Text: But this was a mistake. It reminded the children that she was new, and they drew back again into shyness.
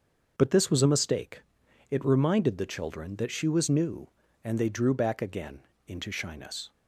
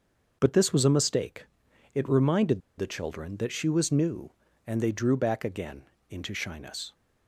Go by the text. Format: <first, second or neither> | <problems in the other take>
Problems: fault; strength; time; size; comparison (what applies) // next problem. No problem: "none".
first | starts louder than the rest; until 1.4 s; 6 dB; also in the first // pauses between "reminded" and "the"; slight; at 2.6 s; 0.17 s long // pauses between "again" and "into"; slight; at 5.8 s; 0.28 s long; slight in the first